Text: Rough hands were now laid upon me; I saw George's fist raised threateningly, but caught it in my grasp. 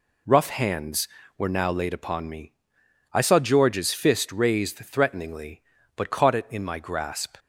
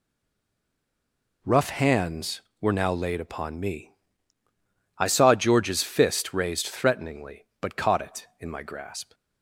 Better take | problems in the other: first | stays silent before the first word; noticeable; until 1.4 s; 1.4 s long

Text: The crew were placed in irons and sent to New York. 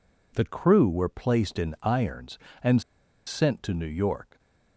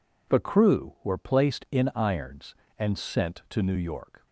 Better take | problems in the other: second | pauses between "and" and "sent"; noticeable; at 2.8 s; 0.46 s long

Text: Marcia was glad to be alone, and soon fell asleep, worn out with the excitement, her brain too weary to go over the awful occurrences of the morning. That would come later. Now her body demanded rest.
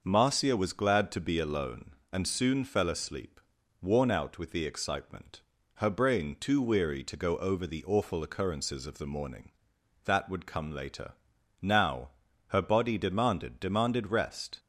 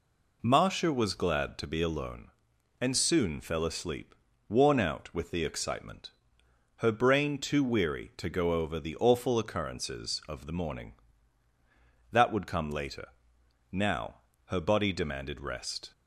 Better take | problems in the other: second | starts louder than the rest; noticeable; until 1.0 s; 6 dB // pauses between "Now" and "her"; at 12.0 s; 0.38 s long; slight in the second // says "demanded" twice; at 13.6 s

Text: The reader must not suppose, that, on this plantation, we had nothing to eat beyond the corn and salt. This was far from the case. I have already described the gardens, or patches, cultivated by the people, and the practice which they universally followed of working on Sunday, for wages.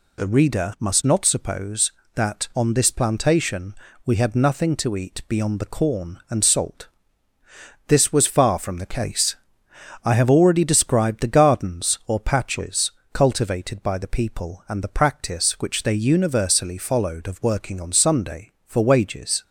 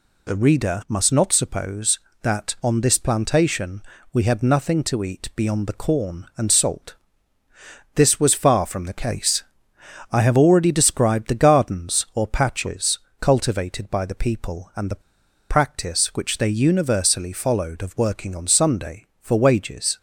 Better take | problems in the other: first | pauses between "the" and "practice"; noticeable; at 15.0 s; 0.48 s long

